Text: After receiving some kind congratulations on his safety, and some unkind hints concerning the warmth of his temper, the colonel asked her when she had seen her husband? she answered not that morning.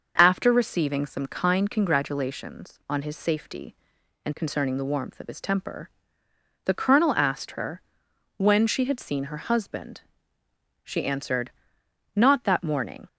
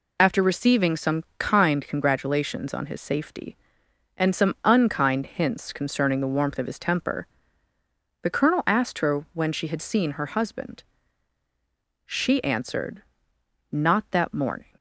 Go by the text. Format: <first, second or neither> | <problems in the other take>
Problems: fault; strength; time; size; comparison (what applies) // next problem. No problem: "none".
second | starts louder than the rest; until 1.1 s; 6 dB // skips "some unkind hints"; at 4.3 s // pauses between "her" and "when"; noticeable; at 7.8 s; 0.56 s long // pauses between "answered" and "not"; noticeable; at 11.5 s; 0.64 s long; noticeable in the second